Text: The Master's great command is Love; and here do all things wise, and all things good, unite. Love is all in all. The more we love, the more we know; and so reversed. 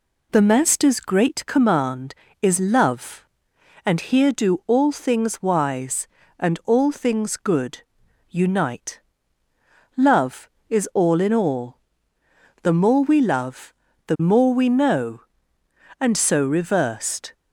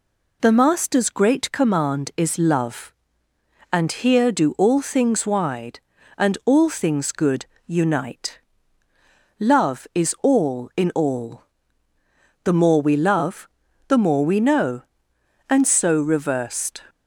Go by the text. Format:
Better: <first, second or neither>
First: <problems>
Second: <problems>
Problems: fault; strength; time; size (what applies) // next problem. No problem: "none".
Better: first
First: none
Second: says "wide" for "wise"; at 5.2 s